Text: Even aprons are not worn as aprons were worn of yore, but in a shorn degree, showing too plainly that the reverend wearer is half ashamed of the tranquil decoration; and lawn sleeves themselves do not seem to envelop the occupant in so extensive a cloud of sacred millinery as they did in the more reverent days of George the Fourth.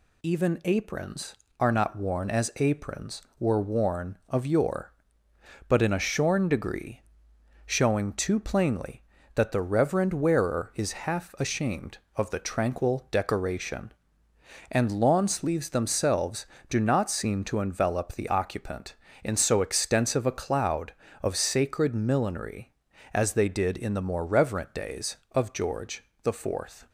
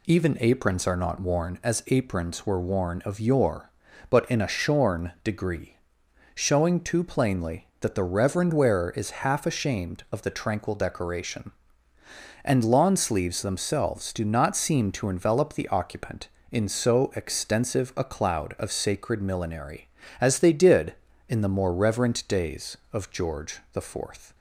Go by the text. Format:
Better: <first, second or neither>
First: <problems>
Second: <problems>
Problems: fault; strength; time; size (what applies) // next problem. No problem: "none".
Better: neither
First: pauses between "George" and "the"; slight; at 26.0 s; 0.20 s long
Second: pauses between "George" and "the"; slight; at 23.5 s; 0.16 s long